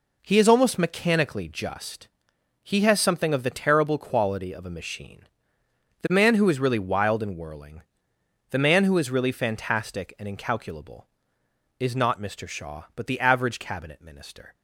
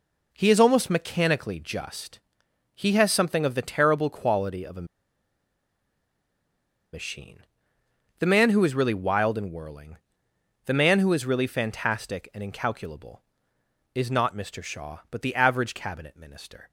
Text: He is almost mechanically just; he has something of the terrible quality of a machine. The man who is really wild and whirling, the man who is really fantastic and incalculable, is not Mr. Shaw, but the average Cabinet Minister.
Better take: first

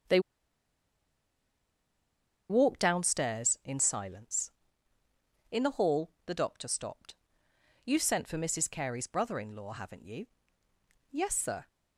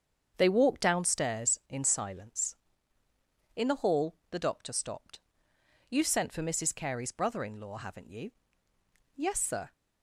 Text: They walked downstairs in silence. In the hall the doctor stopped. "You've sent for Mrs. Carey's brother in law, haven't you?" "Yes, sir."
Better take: second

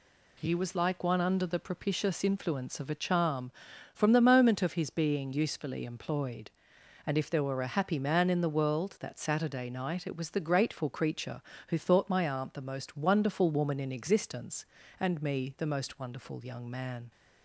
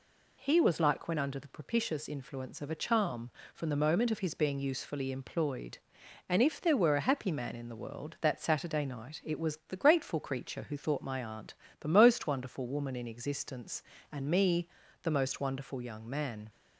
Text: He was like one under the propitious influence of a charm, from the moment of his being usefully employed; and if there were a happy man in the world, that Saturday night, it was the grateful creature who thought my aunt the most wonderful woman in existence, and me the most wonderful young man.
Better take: first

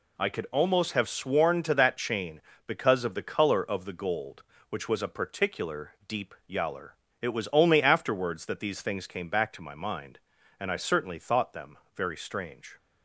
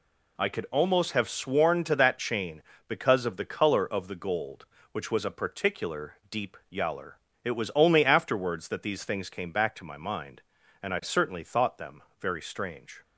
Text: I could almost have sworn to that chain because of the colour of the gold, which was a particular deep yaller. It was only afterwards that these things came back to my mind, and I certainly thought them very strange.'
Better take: neither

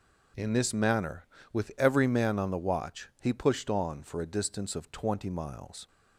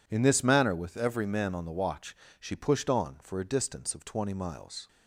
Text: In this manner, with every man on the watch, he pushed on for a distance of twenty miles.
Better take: first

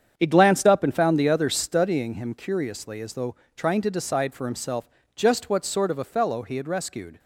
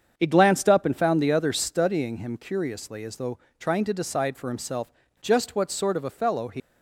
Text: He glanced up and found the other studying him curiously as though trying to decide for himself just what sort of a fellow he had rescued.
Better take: first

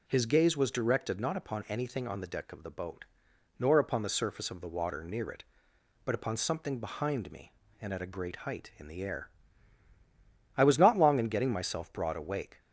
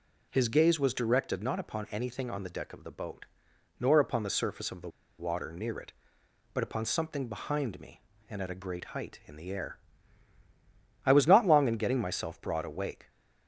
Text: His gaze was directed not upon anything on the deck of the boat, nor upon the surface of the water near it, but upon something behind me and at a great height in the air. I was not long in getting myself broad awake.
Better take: first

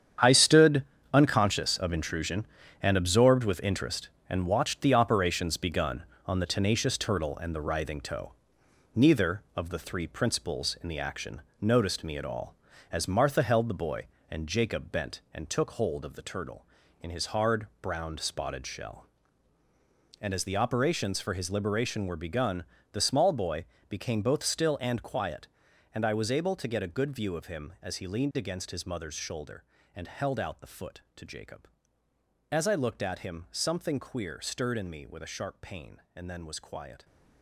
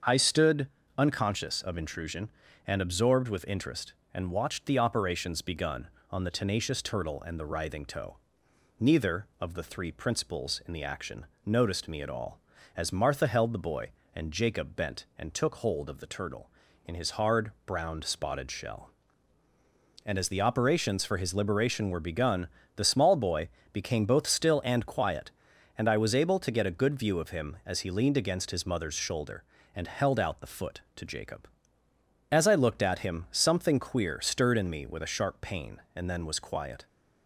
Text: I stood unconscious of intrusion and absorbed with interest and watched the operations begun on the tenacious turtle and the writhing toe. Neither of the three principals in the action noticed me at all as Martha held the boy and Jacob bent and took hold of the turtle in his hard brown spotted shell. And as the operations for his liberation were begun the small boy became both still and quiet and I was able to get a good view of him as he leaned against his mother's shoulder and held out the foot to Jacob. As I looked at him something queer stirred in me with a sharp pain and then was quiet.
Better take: second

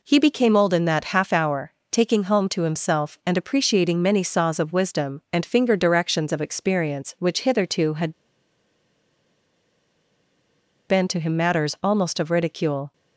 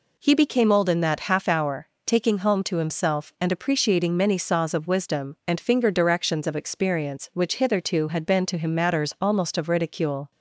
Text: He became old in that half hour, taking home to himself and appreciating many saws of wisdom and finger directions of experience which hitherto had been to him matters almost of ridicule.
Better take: second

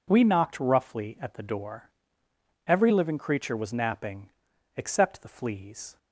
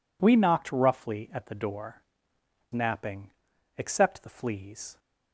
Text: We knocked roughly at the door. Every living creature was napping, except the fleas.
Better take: first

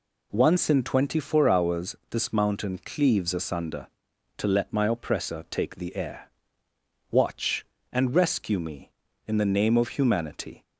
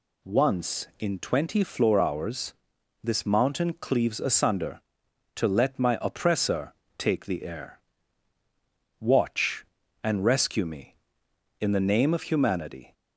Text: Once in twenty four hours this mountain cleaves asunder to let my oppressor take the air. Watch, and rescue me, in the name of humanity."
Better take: first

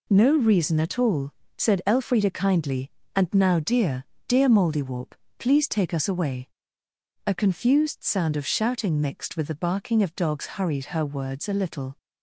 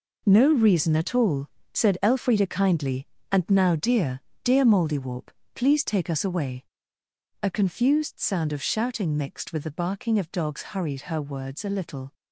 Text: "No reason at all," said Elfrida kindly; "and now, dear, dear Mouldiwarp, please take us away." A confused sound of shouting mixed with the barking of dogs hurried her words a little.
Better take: first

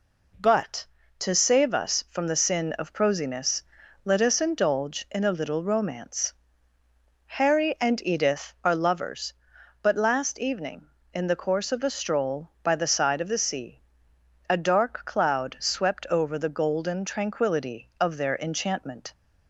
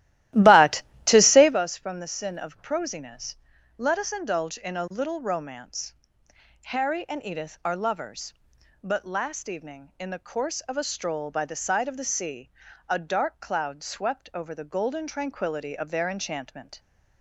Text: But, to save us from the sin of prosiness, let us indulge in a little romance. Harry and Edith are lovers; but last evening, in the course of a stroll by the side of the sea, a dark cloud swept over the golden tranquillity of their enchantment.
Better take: first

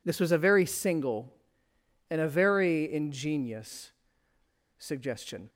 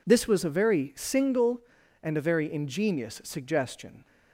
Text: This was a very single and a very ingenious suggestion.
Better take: second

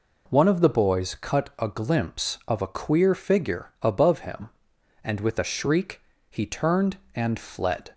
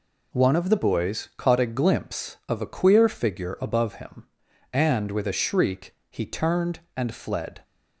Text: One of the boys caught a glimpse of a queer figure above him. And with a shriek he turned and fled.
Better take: second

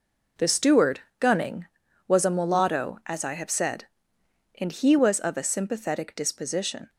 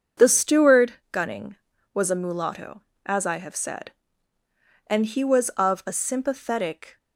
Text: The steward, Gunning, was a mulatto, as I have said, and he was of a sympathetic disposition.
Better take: first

